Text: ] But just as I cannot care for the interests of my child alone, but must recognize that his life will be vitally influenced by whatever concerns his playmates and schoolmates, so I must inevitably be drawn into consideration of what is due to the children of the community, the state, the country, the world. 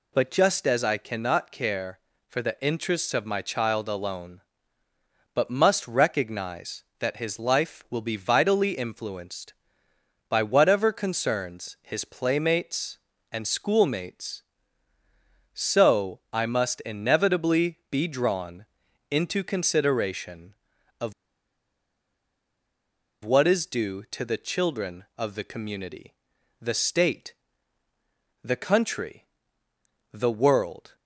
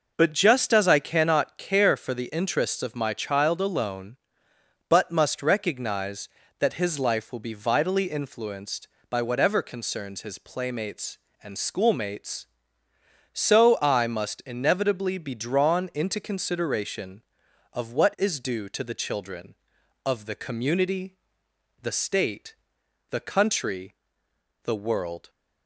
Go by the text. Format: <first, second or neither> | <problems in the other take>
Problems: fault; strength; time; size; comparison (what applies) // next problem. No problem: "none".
second | pauses between "drawn" and "into"; at 18.6 s; 0.44 s long // pauses between "of" and "what"; strong; at 21.1 s; 2.1 s long